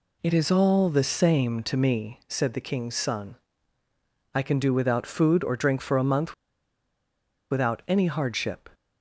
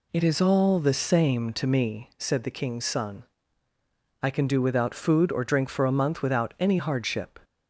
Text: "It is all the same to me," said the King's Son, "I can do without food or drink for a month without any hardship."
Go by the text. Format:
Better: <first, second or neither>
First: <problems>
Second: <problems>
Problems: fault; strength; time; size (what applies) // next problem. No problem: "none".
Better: second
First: pauses between "month" and "without"; at 6.3 s; 1.1 s long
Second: none